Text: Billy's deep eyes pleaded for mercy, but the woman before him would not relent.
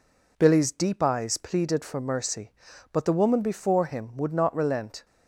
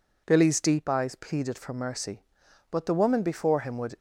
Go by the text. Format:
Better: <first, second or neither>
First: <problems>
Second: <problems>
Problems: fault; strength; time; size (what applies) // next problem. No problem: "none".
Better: first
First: none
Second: stops before "not relent"; at 3.9 s